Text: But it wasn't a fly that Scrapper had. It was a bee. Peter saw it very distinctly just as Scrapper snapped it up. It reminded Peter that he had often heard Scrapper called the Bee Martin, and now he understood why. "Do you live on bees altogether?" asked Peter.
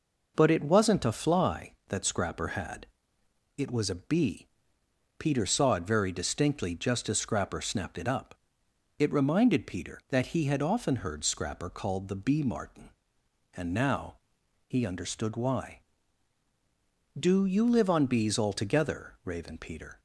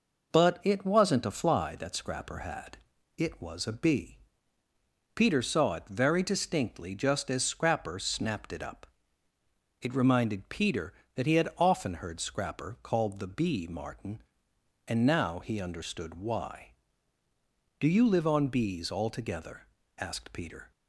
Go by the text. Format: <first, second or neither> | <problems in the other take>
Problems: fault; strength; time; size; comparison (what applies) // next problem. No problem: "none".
second | pauses between "now" and "he"; noticeable; at 14.1 s; 0.52 s long // says "raven" for "asked"; at 19.2 s